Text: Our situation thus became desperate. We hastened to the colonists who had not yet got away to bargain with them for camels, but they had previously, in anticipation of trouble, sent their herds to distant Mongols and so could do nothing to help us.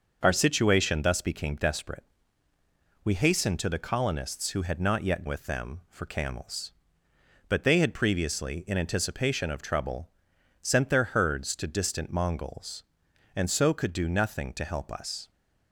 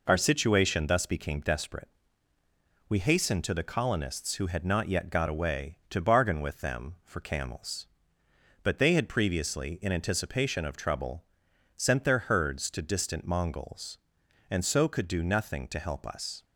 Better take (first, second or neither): second